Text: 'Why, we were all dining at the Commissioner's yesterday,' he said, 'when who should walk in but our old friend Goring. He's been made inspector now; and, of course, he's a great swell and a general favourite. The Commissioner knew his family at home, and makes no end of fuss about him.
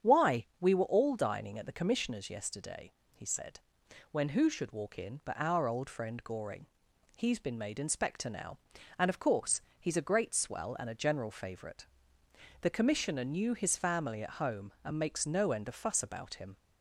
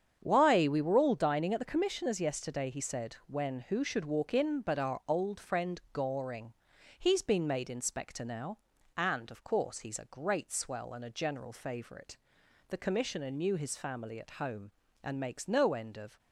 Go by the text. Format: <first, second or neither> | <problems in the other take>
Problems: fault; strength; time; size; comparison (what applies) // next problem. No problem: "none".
first | starts louder than the rest; strong; until 1.2 s; 8 dB; strong in the first // stops before "fuss about him"; at 16.1 s